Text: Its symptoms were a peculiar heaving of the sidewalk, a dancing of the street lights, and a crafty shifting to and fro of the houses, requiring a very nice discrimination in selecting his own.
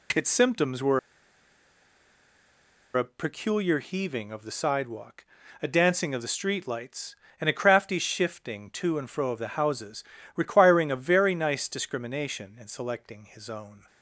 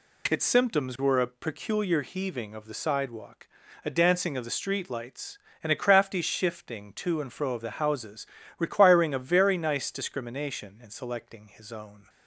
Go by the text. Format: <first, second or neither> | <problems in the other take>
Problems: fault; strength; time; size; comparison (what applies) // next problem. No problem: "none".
second | pauses between "were" and "a"; strong; at 0.9 s; 1.9 s long